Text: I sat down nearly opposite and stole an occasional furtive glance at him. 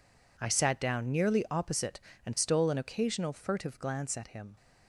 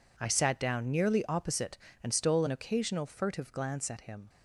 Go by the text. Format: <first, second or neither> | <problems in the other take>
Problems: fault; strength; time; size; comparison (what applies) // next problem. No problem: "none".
neither | none